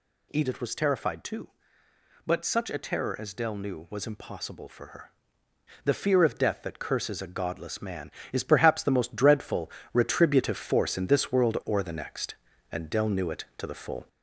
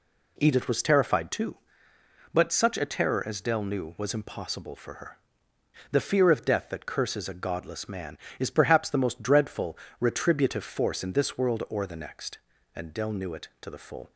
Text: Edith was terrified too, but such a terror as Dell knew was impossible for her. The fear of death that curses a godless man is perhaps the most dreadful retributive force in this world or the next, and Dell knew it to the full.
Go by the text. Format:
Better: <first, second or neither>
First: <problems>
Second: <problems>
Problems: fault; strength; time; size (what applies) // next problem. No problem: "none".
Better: second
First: gets louder; throughout; 4 dB // pauses between "dreadful" and "retributive"; slight; at 9.6 s; 0.24 s long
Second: pauses between "dreadful" and "retributive"; slight; at 9.7 s; 0.24 s long